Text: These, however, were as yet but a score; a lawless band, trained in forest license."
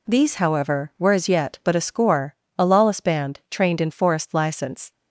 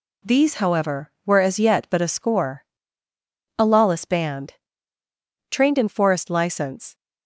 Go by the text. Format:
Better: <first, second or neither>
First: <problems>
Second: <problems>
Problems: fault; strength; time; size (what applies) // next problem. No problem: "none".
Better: neither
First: none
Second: none